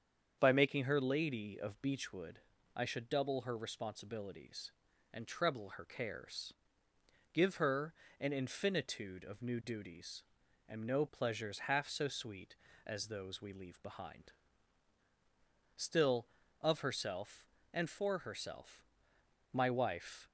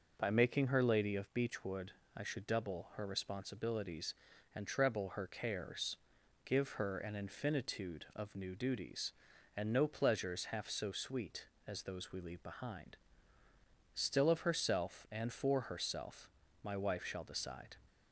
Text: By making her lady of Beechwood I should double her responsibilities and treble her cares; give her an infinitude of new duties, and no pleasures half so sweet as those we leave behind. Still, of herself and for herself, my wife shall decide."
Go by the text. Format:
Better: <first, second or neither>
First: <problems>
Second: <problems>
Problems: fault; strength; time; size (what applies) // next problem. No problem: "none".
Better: second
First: starts louder than the rest; strong; until 1.4 s; 7.5 dB // pauses between "Beechwood" and "I"; slight; at 2.3 s; 0.34 s long // pauses between "her" and "an"; slight; at 7.9 s; 0.28 s long // stops before "shall decide"; at 20.2 s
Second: pauses between "Beechwood" and "I"; slight; at 1.9 s; 0.24 s long